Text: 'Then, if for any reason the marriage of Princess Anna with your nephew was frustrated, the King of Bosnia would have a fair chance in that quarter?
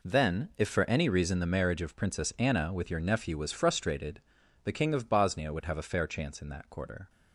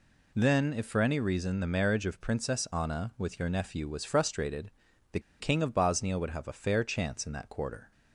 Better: first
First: none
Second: pauses between "the" and "King"; slight; at 5.1 s; 0.21 s long

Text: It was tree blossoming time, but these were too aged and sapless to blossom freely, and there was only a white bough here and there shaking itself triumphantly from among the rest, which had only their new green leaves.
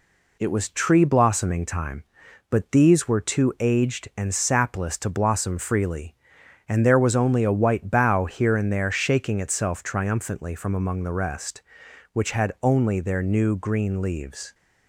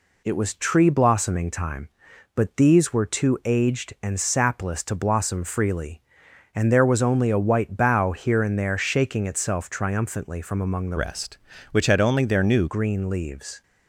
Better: first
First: none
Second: changes voice from "rest" to "new"; from 10.9 to 12.6 s; 1.7 s long

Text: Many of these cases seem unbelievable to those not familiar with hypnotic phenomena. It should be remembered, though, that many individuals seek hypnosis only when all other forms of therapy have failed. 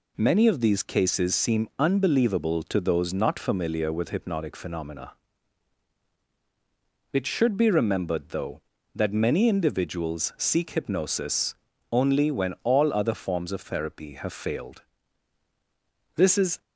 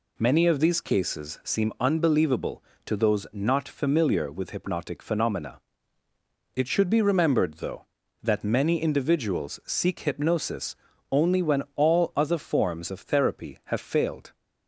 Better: second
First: pauses between "hypnosis" and "only"; slight; at 11.5 s; 0.36 s long // goes on to say "This is"; slight; from 16.1 s on; 0.44 s long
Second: pauses between "hypnosis" and "only"; slight; at 10.7 s; 0.34 s long

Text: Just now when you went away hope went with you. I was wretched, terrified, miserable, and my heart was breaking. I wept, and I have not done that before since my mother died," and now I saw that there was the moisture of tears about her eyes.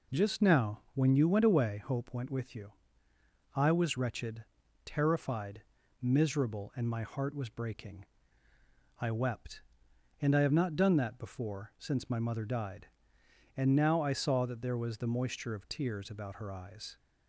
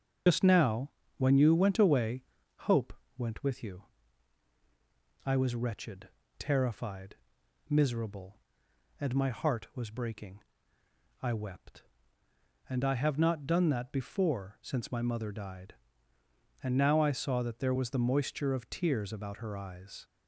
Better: first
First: pauses between "now" and "when"; slight; at 0.7 s; 0.16 s long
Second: loses the start of "Just"; at 0.2 s; 60 ms // starts louder than the rest; until 1.5 s; 6.5 dB // pauses between "now" and "when"; slight; at 0.9 s; 0.26 s long // pauses between "away" and "hope"; noticeable; at 2.2 s; 0.46 s long // pauses between "hope" and "went"; slight; at 2.9 s; 0.24 s long

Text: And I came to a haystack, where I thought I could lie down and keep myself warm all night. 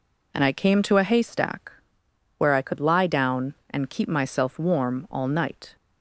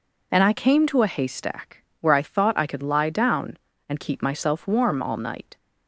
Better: second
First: skips "thought I"; at 2.6 s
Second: none

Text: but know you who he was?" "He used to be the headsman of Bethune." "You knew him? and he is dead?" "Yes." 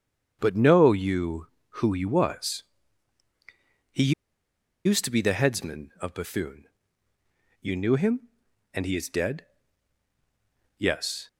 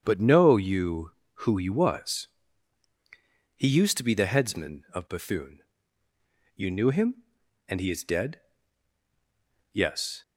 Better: second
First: starts louder than the rest; strong; until 1.4 s; 8 dB // pauses between "He" and "used"; noticeable; at 4.1 s; 0.73 s long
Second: starts louder than the rest; strong; until 1.0 s; 8 dB

